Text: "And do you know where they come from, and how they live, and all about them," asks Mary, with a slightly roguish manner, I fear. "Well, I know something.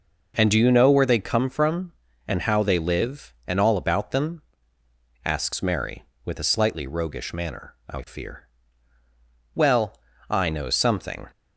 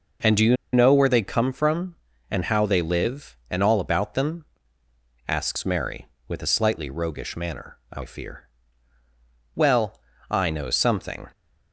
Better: first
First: none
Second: pauses between "you" and "know"; slight; at 0.5 s; 0.18 s long

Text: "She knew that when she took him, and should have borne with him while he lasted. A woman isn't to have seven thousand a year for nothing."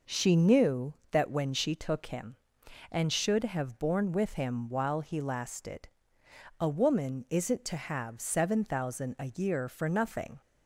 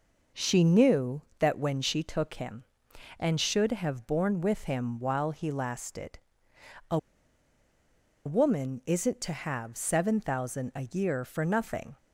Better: first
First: none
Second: pauses between "A" and "woman"; strong; at 6.9 s; 1.2 s long

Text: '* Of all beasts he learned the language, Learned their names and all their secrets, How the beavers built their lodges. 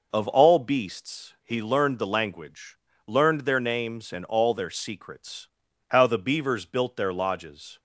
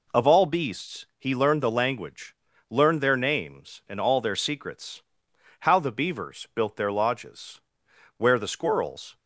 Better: first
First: none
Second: goes on to say "Where the squirrels"; noticeable; from 8.1 s on; 1.0 s long

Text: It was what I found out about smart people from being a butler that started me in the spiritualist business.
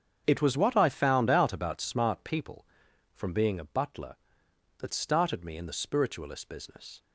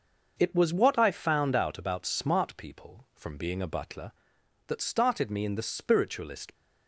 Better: first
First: starts louder than the rest; strong; until 1.2 s; 7.5 dB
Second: starts louder than the rest; until 1.4 s; 6 dB // stops before "business"; at 6.5 s

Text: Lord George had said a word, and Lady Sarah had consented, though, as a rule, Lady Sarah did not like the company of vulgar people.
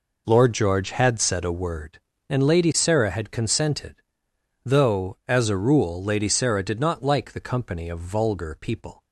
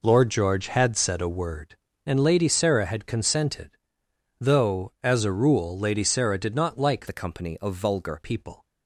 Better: first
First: none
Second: changes voice from "the" to "vulgar"; from 7.0 to 8.2 s; 1.2 s long

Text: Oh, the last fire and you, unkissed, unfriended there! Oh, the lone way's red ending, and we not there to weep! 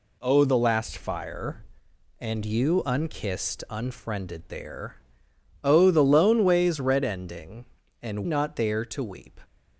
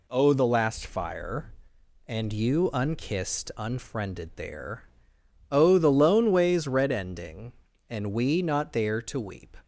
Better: second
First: skips "we"; at 8.2 s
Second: none

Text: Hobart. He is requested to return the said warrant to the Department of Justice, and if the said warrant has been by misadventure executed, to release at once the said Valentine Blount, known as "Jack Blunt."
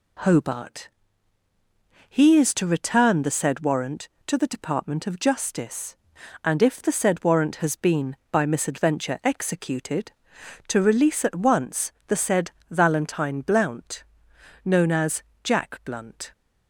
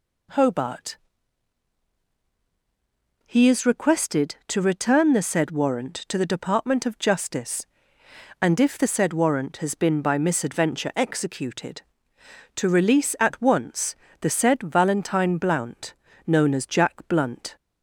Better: second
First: skips "requested"; at 2.5 s // pauses between "once" and "the"; slight; at 11.9 s; 0.16 s long // pauses between "said" and "Valentine"; slight; at 12.4 s; 0.18 s long // pauses between "as" and "Jack"; slight; at 15.2 s; 0.22 s long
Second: pauses between "once" and "the"; slight; at 13.9 s; 0.24 s long

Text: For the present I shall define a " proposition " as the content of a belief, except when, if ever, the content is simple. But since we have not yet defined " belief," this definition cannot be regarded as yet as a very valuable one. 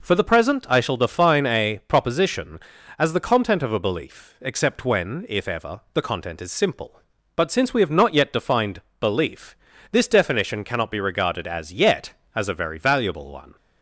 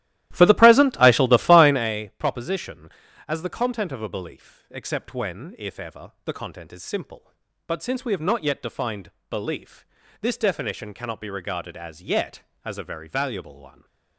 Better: first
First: none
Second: starts louder than the rest; strong; until 1.9 s; 14 dB

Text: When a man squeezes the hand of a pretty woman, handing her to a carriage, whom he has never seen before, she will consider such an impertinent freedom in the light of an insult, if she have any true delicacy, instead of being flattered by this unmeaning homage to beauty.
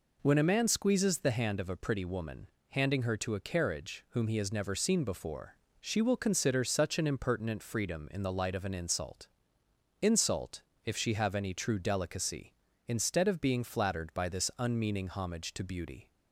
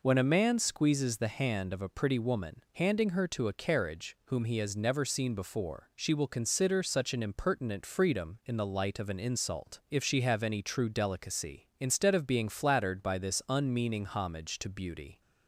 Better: second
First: says "insult" twice; at 10.0 s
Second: none

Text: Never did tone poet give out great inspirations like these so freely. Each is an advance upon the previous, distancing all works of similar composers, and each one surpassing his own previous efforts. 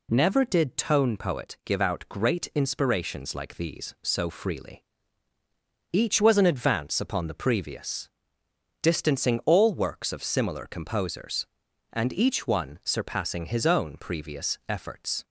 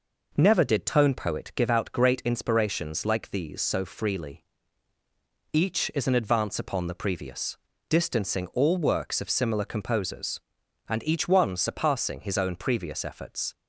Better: second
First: says "was" for "is"; at 6.1 s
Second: none

